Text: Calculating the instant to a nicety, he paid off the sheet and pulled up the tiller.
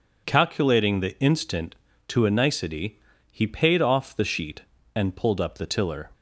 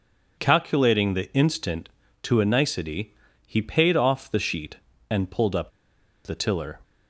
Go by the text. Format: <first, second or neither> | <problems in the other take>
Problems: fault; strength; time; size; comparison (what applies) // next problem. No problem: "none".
first | pauses between "up" and "the"; noticeable; at 5.7 s; 0.55 s long